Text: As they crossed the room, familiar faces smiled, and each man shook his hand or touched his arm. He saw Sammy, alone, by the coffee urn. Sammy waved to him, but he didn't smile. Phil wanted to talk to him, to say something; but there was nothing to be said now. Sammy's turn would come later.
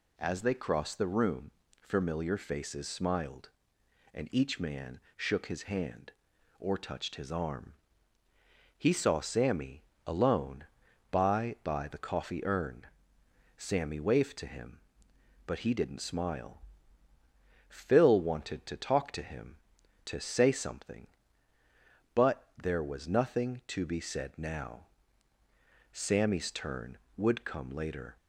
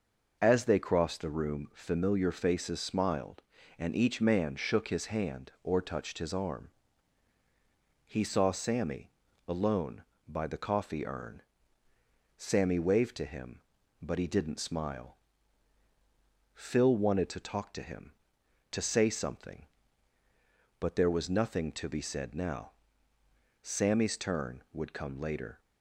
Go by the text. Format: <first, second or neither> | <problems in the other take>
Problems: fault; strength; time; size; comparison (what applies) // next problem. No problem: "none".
second | pauses between "man" and "shook"; slight; at 5.0 s; 0.16 s long // says "by" twice; at 11.6 s